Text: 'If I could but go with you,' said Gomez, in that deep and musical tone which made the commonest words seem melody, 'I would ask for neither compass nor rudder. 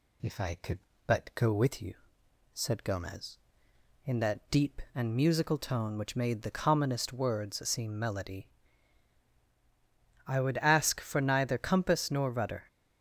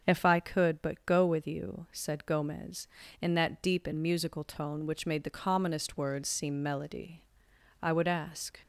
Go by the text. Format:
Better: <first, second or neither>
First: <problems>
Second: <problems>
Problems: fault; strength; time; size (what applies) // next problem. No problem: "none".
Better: first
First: none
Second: starts louder than the rest; until 1.0 s; 6.5 dB // stops before "for neither compass nor rudder"; at 8.6 s